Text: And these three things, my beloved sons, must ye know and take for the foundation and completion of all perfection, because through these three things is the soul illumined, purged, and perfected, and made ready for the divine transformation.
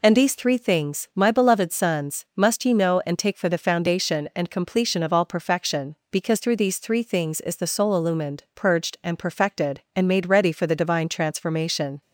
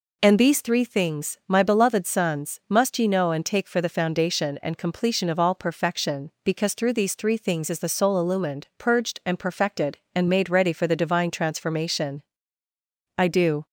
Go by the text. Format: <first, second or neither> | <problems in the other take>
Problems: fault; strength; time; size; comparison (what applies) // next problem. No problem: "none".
first | goes on to say "I do"; slight; from 13.1 s on; 0.48 s long